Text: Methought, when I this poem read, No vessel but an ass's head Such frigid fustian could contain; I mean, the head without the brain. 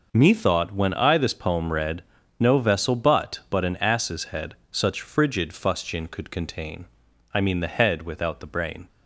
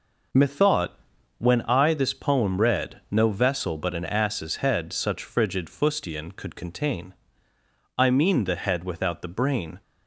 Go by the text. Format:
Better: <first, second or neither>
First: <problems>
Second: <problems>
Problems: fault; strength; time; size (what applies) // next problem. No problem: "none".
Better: second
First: says "but" twice; at 3.4 s // pauses between "head" and "Such"; slight; at 4.5 s; 0.16 s long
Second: none